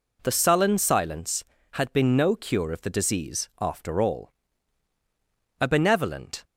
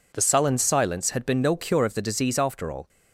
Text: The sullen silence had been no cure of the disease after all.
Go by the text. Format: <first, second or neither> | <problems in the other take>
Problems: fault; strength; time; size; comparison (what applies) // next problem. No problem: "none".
second | goes on to say "A benevolent"; noticeable; from 5.5 s on; 0.84 s long